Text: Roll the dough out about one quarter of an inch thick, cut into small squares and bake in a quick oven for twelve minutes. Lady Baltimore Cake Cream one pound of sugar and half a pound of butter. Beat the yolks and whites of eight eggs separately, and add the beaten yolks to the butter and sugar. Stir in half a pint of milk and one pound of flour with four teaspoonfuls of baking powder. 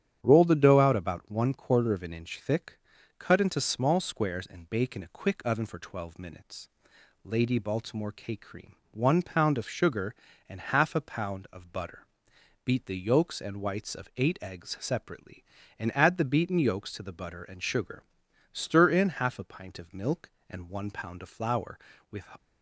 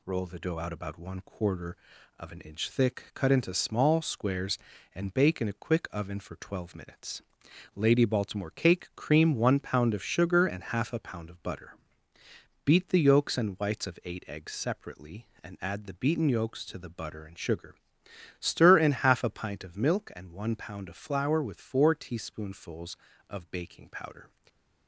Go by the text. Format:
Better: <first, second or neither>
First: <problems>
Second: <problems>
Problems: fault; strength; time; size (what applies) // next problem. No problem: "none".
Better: second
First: starts louder than the rest; strong; until 1.2 s; 9.5 dB // pauses between "Cream" and "one"; slight; at 8.7 s; 0.16 s long // stops before "four teaspoonfuls of baking powder"; at 22.3 s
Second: none